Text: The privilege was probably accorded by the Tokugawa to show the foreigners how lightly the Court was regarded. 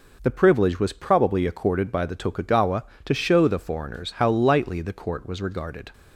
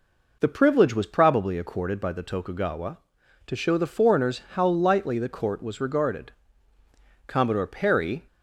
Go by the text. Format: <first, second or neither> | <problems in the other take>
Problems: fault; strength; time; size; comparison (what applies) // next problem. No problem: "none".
first | goes on to say "Commodore Perry"; noticeable; from 7.2 s on; 1.0 s long